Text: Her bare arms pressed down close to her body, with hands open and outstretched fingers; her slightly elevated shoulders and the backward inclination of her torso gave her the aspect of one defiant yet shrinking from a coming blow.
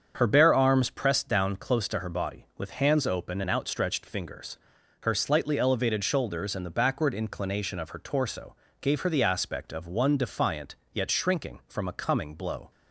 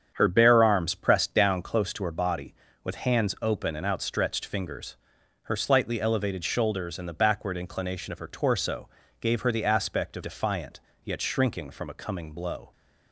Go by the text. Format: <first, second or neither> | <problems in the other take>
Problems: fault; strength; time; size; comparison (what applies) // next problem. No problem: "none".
first | starts louder than the rest; strong; until 1.1 s; 8 dB; strong in the first // pauses between "torso" and "gave"; slight; at 8.8 s; 0.32 s long; slight in the first // skips "one"; at 10.2 s // pauses between "defiant" and "yet"; slight; at 10.7 s; 0.24 s long; slight in the first